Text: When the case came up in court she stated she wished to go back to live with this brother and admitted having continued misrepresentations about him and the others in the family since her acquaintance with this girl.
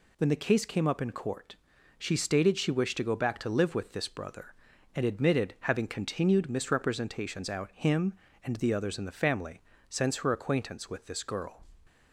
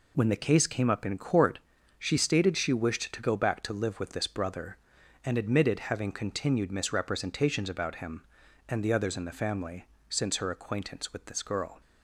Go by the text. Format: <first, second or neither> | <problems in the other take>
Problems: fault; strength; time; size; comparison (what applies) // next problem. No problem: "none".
second | pauses between "court" and "she"; at 1.5 s; 0.42 s long; also in the second // says "out" for "about"; at 7.4 s // pauses between "family" and "since"; slight; at 9.6 s; 0.28 s long; slight in the second